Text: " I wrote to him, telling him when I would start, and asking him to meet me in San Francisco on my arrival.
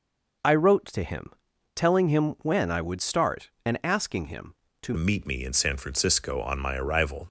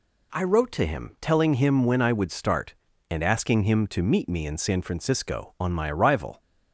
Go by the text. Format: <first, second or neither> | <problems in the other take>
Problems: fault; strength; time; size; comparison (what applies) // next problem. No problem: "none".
second | changes voice at "meet"; from 4.9 s on; 2.3 s long